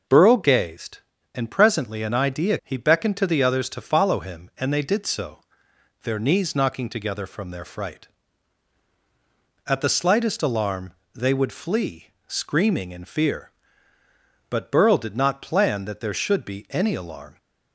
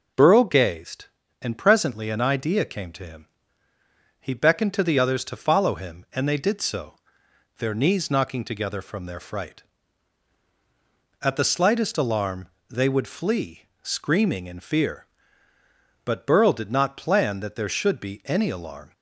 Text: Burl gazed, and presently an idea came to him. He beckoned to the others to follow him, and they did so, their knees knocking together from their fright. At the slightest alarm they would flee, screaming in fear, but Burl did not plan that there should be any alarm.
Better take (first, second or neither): second